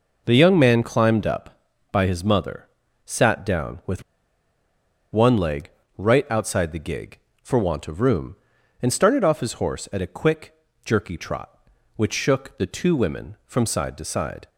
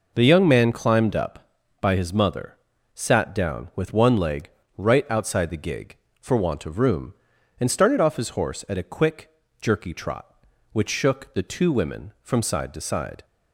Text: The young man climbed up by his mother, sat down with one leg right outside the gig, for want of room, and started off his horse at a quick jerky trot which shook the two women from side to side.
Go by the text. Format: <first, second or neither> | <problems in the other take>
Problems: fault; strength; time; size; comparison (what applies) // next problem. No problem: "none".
second | pauses between "with" and "one"; at 4.0 s; 1.0 s long // pauses between "leg" and "right"; slight; at 5.6 s; 0.30 s long; slight in the second // pauses between "quick" and "jerky"; slight; at 10.5 s; 0.30 s long; slight in the second